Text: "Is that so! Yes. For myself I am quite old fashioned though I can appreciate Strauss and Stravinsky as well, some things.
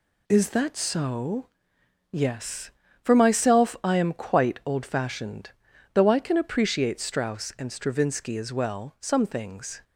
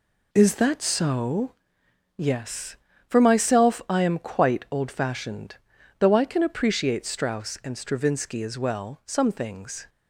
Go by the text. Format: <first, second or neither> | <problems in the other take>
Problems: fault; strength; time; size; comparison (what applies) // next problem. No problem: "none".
first | starts louder than the rest; slight; until 1.8 s; 2.5 dB // pauses between "fashioned" and "though"; at 5.5 s; 0.42 s long; also in the first